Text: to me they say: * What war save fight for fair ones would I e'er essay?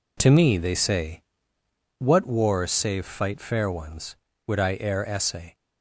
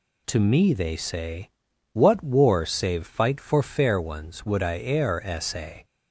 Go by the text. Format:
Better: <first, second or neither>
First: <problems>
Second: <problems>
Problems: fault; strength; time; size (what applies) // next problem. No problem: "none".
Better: second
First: skips "for"; at 3.4 s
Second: none